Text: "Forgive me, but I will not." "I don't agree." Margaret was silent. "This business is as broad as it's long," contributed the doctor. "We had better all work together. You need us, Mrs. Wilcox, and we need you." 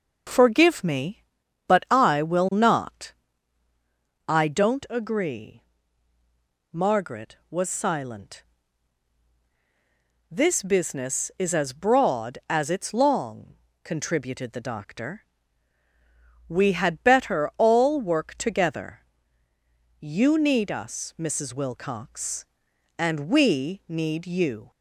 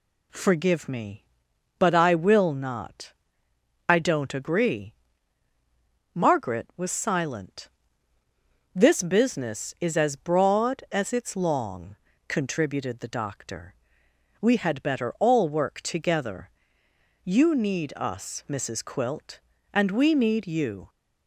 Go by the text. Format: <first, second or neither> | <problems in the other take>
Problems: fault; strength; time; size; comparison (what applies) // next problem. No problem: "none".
first | says "Quilt" for "Wilcox"; at 18.8 s